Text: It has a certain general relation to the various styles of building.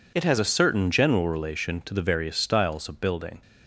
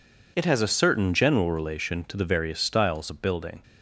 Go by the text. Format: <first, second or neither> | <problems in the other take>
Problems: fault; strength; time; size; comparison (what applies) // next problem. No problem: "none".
neither | none